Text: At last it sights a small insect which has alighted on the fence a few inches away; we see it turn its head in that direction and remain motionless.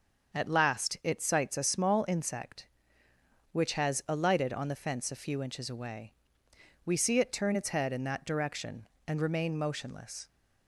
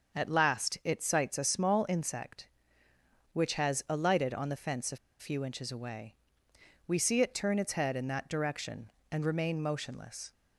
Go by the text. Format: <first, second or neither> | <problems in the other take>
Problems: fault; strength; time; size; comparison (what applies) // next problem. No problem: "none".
first | starts louder than the rest; until 1.2 s; 6.5 dB; also in the first // pauses between "a" and "few"; slight; at 4.9 s; 0.22 s long